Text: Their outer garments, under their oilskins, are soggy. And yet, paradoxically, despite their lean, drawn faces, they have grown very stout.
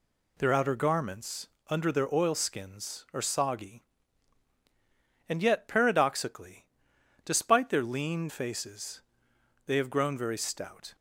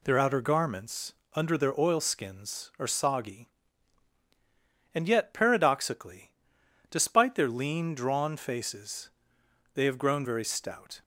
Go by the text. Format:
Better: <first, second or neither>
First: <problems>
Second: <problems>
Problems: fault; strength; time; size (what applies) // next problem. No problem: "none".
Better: second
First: skips "drawn"; at 8.2 s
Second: none